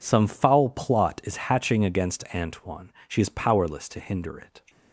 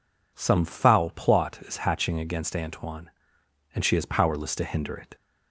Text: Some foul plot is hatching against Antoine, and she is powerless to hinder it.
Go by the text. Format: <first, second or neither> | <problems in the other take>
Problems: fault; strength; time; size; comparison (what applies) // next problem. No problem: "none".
second | skips "and"; at 2.9 s